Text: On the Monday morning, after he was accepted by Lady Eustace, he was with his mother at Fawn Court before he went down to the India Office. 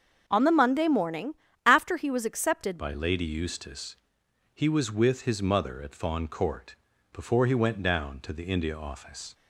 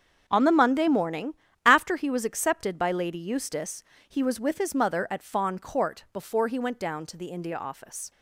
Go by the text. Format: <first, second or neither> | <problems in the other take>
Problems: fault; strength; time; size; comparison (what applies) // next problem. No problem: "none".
second | starts louder than the rest; until 1.2 s; 7 dB; also in the second // changes voice at "by"; from 2.7 s on; 6.6 s long // pauses between "Court" and "before"; at 6.7 s; 0.38 s long